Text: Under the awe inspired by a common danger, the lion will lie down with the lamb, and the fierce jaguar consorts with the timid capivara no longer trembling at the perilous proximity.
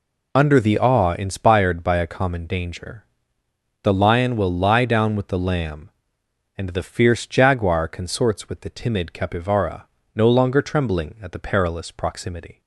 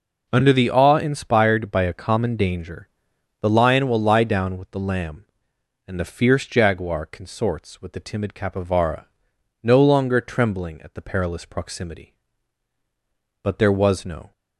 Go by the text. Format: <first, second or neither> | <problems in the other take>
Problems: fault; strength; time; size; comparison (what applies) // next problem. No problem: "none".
first | pauses between "capivara" and "no"; noticeable; at 9.0 s; 0.58 s long; slight in the first // goes on to say "But there was no"; noticeable; from 13.4 s on; 0.88 s long